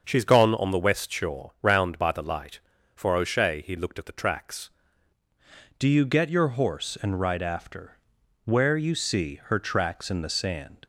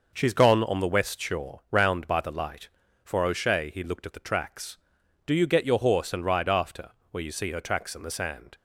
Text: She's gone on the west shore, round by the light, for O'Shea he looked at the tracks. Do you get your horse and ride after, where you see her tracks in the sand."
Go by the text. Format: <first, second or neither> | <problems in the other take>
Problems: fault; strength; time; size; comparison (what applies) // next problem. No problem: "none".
second | starts louder than the rest; until 1.0 s; 6.5 dB // changes voice at "Do"; from 5.7 s on; 5.0 s long